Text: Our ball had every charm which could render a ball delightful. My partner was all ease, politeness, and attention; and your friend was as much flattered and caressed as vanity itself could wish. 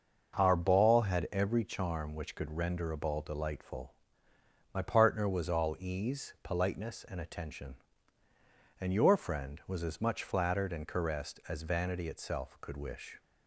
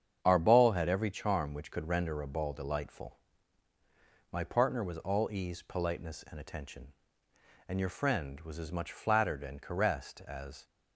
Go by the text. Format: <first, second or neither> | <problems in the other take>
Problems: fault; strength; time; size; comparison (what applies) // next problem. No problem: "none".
first | starts louder than the rest; strong; until 1.2 s; 8 dB // stops before "vanity itself could wish"; at 10.6 s